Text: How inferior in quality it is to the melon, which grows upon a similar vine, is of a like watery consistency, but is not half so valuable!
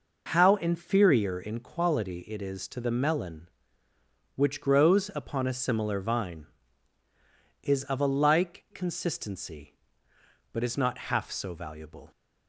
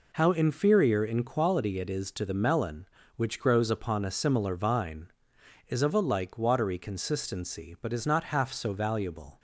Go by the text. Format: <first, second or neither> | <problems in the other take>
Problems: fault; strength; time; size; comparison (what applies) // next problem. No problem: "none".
second | skips "watery"; at 8.6 s